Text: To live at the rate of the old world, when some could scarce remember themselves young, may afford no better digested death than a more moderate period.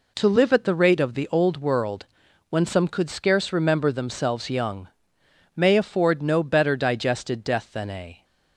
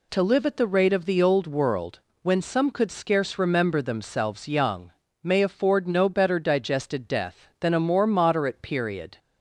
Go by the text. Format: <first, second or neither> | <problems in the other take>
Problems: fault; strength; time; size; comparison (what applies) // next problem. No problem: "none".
second | stops before "more moderate period"; at 8.2 s